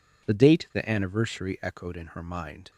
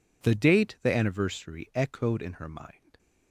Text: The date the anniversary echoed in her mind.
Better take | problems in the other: neither | none

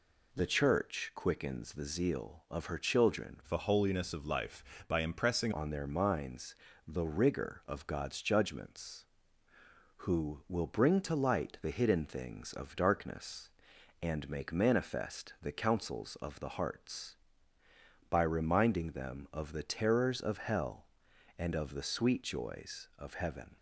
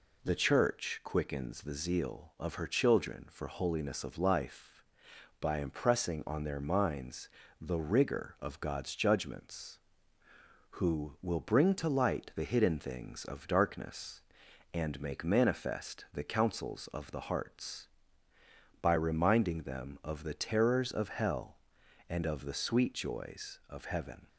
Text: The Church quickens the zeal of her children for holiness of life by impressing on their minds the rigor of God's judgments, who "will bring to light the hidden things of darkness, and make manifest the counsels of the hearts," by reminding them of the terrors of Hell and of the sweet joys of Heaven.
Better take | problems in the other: second | changes voice from "for" to "impressing"; from 3.4 to 5.5 s; 2.1 s long // pauses between "minds" and "the"; slight; at 6.5 s; 0.28 s long; slight in the second

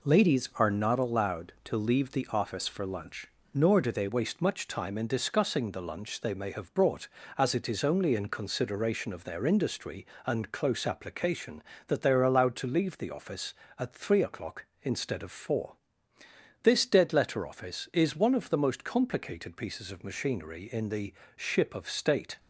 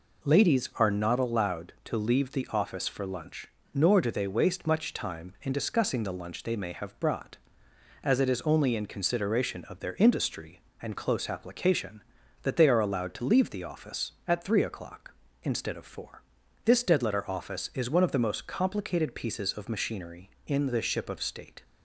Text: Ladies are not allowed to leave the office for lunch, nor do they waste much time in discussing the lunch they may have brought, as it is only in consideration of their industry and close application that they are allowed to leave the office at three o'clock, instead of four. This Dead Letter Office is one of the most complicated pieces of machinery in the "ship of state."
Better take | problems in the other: second | changes voice at "waste"; from 4.0 s on; 18.3 s long // pauses between "the" and "ship"; slight; at 21.1 s; 0.24 s long

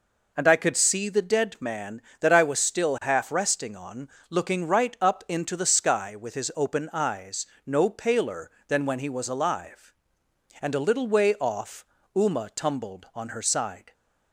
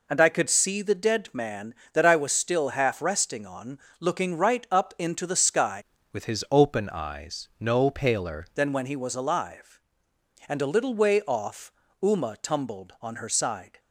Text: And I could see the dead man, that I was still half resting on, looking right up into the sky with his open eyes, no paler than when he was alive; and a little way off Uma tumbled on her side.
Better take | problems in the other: first | changes voice from "with" to "paler"; from 6.1 to 8.4 s; 2.3 s long // pauses between "off" and "Uma"; slight; at 11.7 s; 0.28 s long; slight in the first

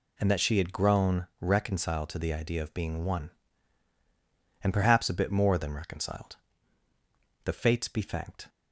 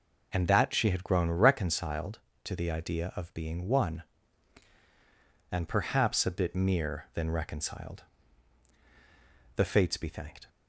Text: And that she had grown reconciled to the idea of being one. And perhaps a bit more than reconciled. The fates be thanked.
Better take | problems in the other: first | says "mere" for "more"; at 6.5 s

